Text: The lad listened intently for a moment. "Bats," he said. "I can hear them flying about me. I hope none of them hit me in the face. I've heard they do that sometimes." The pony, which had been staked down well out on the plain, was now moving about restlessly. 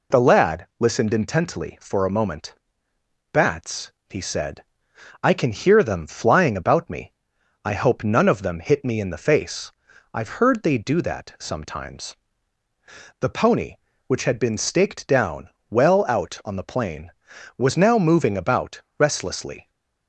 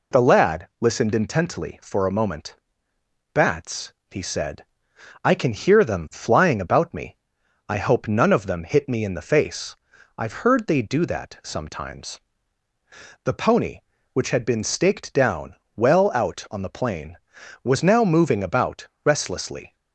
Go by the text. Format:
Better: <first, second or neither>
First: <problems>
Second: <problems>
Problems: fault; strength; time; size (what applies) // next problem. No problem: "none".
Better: neither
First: pauses between "down" and "well"; slight; at 15.4 s; 0.20 s long // pauses between "about" and "restlessly"; slight; at 18.8 s; 0.16 s long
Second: pauses between "down" and "well"; slight; at 15.5 s; 0.20 s long // pauses between "about" and "restlessly"; slight; at 18.8 s; 0.16 s long